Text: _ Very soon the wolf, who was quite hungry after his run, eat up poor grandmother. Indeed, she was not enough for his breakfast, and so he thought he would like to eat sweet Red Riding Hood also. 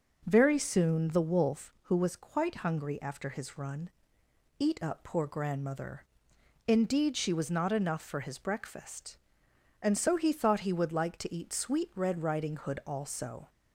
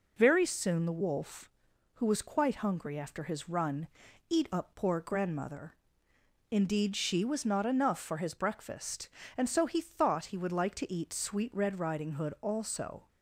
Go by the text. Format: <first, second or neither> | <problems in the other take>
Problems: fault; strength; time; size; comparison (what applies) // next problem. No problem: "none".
neither | none